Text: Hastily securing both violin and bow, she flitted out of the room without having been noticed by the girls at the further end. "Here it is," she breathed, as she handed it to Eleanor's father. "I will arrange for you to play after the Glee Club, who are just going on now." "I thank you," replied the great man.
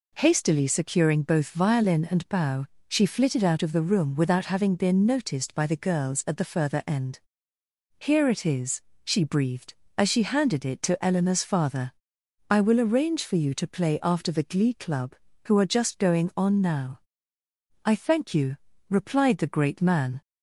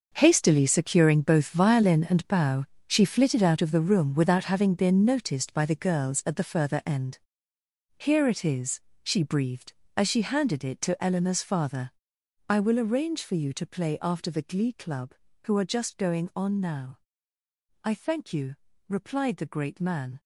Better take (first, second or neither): first